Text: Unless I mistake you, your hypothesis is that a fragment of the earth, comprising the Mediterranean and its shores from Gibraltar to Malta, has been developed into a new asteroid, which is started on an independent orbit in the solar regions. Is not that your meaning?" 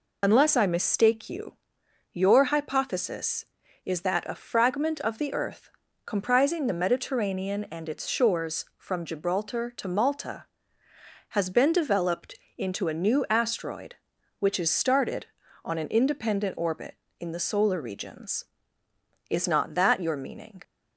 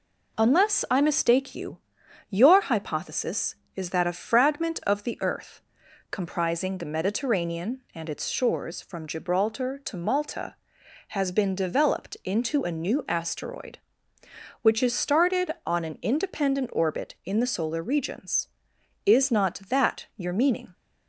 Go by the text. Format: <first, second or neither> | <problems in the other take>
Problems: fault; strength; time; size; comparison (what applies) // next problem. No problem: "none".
second | loses the start of "Unless"; at 0.2 s; 65 ms // pauses between "developed" and "into"; slight; at 12.3 s; 0.24 s long